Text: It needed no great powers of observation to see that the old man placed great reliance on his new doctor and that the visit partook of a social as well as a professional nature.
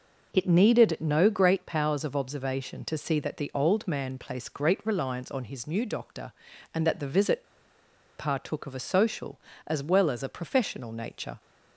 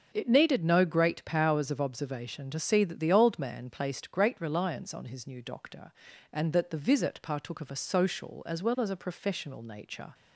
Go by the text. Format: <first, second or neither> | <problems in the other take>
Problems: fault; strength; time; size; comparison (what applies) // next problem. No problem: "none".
second | pauses between "visit" and "partook"; noticeable; at 7.4 s; 0.74 s long